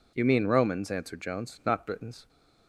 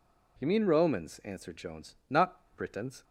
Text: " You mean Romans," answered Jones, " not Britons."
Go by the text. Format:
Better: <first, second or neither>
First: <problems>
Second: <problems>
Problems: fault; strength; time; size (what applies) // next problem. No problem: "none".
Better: neither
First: none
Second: none